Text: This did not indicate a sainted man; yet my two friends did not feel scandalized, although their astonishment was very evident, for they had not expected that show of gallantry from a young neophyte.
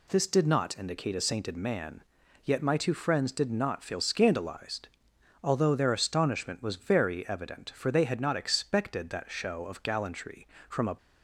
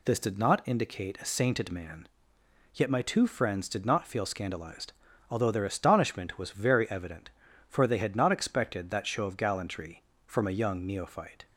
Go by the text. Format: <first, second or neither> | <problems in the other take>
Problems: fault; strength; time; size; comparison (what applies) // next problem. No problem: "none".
second | stops before "young neophyte"; at 10.9 s